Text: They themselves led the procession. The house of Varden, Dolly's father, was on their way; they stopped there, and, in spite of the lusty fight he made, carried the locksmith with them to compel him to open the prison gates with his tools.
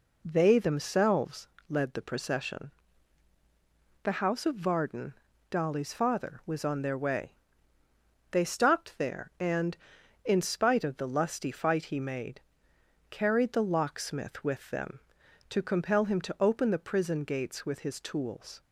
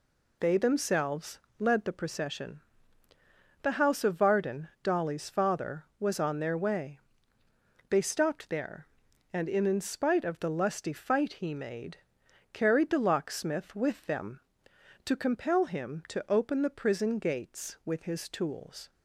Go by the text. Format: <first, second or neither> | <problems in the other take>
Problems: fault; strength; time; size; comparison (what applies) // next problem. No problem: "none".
first | pauses between "themselves" and "led"; slight; at 1.3 s; 0.18 s long; slight in the first // says "in" twice; at 9.6 s